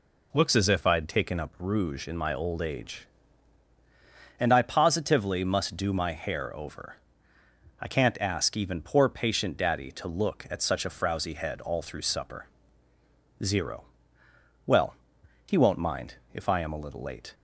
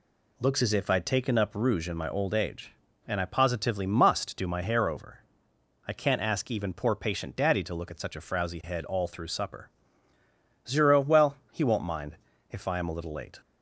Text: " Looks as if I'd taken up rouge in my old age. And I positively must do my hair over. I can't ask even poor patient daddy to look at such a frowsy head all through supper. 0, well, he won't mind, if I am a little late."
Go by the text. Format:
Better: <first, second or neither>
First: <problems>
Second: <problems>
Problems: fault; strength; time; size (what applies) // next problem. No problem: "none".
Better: neither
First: none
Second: none